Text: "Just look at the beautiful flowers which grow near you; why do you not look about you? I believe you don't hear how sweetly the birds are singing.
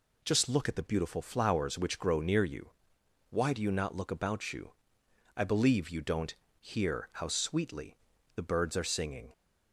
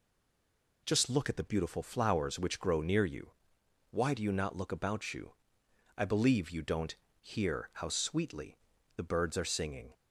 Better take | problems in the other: first | stays silent before the first word; slight; until 0.8 s; 0.8 s long // pauses between "don't" and "hear"; slight; at 6.9 s; 0.24 s long; slight in the first // pauses between "sweetly" and "the"; at 8.5 s; 0.40 s long; also in the first

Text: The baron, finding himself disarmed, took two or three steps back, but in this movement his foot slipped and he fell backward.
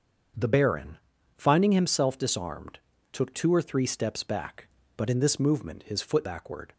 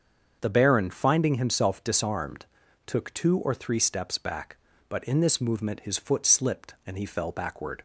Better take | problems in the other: second | starts louder than the rest; until 1.7 s; 7 dB; also in the second // skips "slipped and he fell"; at 6.2 s

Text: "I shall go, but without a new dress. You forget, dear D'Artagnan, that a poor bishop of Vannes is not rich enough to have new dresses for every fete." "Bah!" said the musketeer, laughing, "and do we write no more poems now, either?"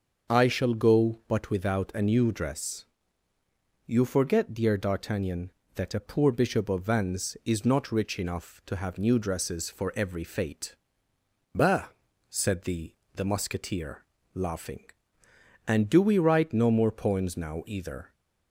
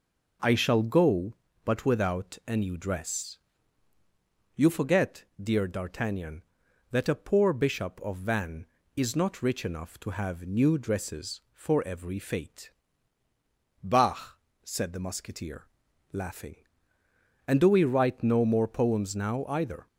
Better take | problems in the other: second | starts louder than the rest; until 1.3 s; 6.5 dB // says "the" twice; at 13.1 s

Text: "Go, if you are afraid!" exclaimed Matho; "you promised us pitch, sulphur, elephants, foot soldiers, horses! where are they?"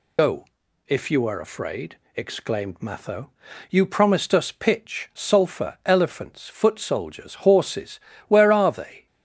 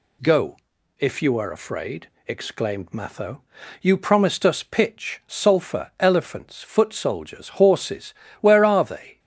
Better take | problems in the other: second | loses the start of "Go"; at 0.1 s; 100 ms

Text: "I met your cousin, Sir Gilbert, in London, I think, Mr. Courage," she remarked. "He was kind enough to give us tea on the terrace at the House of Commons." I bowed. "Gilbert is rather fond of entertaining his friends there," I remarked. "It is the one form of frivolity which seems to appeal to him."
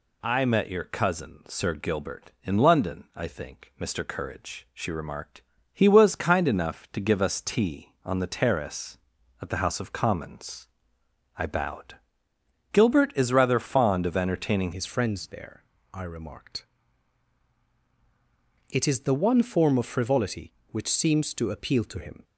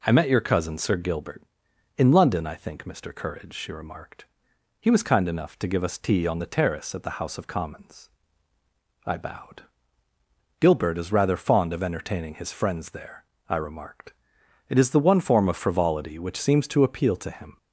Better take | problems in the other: second | changes voice at "his"; from 14.7 s on; 7.5 s long

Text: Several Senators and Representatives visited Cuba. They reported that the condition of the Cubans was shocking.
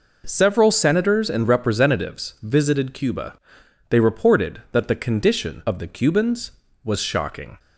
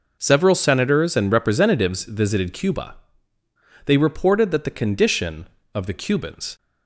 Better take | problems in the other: first | stops before "was shocking"; at 6.5 s

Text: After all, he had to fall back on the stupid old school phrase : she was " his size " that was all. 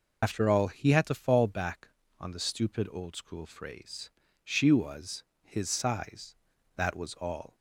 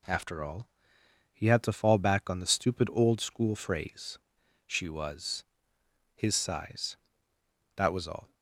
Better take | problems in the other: second | loses the start of "After"; at 0.2 s; 80 ms

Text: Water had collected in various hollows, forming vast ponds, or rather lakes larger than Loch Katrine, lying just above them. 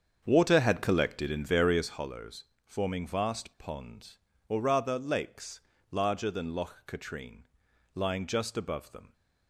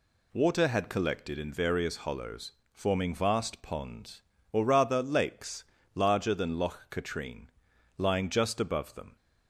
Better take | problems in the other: second | starts louder than the rest; strong; until 2.0 s; 7.5 dB // pauses between "lakes" and "larger"; slight; at 5.6 s; 0.32 s long; slight in the second

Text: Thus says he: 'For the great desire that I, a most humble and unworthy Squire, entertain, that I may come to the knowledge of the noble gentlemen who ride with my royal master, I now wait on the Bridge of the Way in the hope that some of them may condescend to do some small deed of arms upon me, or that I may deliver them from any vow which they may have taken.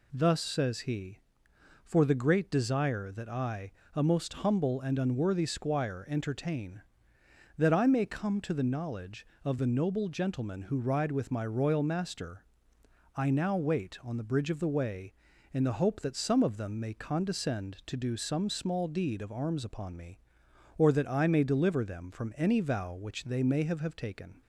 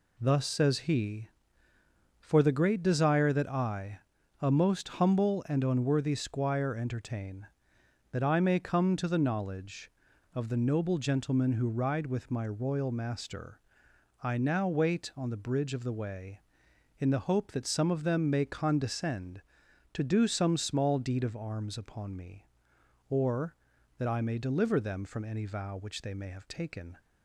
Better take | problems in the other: second | says "have" twice; at 23.8 s

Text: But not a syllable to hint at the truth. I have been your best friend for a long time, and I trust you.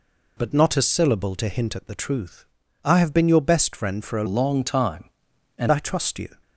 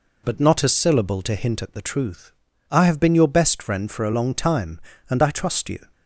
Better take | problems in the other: second | changes voice from "long" to "and"; from 4.2 to 5.7 s; 1.5 s long

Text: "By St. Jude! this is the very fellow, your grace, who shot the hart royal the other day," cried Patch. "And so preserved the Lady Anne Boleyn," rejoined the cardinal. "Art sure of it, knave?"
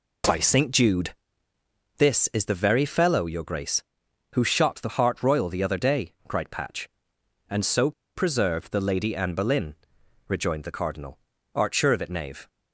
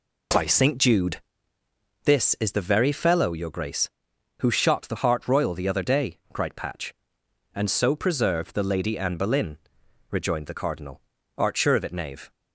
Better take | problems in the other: second | pauses between "so" and "preserved"; slight; at 7.9 s; 0.24 s long

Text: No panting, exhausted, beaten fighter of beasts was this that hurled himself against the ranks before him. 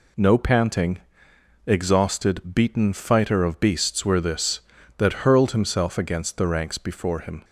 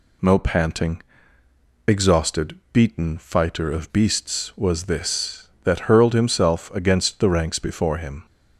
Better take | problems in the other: second | says "were" for "was"; at 4.0 s

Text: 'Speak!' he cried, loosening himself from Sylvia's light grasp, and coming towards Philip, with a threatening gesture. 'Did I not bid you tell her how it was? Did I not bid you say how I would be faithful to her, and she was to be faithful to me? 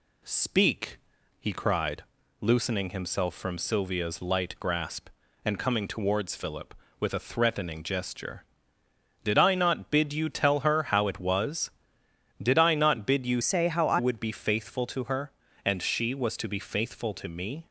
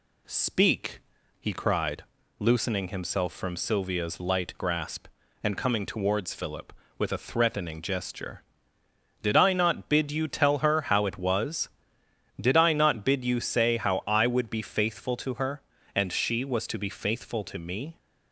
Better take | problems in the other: second | changes voice from "say" to "I"; from 13.4 to 13.9 s; 0.5 s long

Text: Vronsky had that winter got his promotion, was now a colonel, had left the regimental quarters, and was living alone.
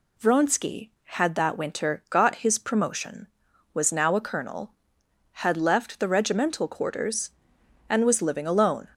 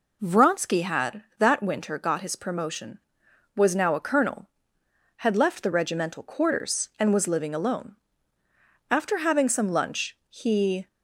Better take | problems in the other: first | goes on to say "After having some lunch he"; strong; from 8.9 s on; 1.9 s long

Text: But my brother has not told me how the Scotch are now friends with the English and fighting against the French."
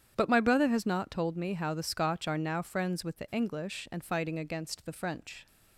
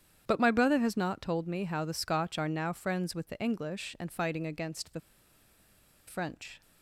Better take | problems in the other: first | starts louder than the rest; strong; until 1.2 s; 9 dB; strong in the first // pauses between "the" and "French"; at 5.0 s; 1.0 s long

